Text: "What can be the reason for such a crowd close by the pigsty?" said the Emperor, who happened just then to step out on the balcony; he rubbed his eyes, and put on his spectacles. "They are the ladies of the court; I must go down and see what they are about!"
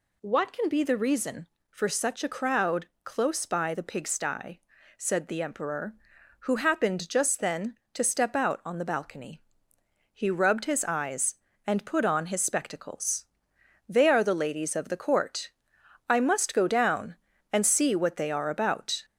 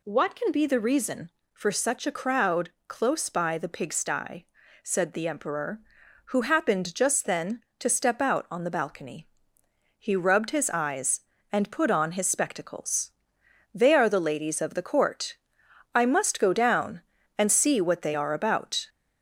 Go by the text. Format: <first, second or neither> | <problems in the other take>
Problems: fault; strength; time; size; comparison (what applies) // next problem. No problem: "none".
neither | pauses between "crowd" and "close"; slight; the same in both